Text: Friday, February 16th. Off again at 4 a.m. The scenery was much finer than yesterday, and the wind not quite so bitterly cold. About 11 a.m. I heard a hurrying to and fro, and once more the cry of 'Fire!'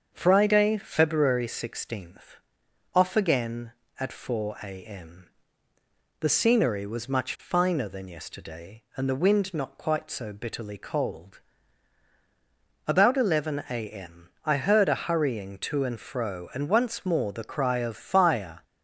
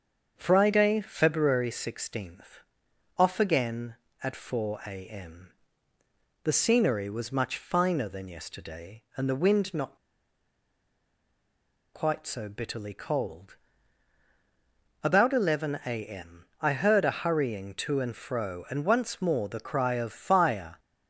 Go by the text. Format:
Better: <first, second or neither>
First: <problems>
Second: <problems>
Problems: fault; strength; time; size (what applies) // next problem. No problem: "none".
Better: first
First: starts louder than the rest; until 1.1 s; 7 dB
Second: starts louder than the rest; until 1.3 s; 7 dB // pauses between "not" and "quite"; strong; at 9.9 s; 1.9 s long